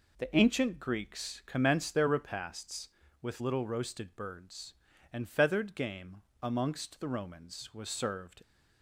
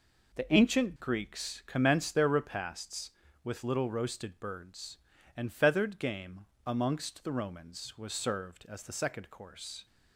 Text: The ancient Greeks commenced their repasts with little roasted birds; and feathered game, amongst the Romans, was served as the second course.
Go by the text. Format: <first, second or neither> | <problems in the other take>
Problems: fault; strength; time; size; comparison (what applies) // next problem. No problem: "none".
second | stops before "as the second course"; at 8.4 s